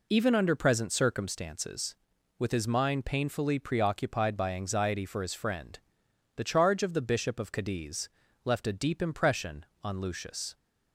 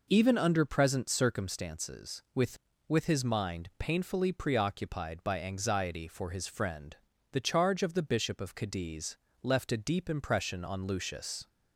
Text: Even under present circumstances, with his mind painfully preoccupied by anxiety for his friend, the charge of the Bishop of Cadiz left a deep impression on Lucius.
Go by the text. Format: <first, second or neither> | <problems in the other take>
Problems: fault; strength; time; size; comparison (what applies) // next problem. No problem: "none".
first | says "with" twice; at 2.8 s // pauses between "Cadiz" and "left"; slight; at 9.1 s; 0.26 s long; slight in the first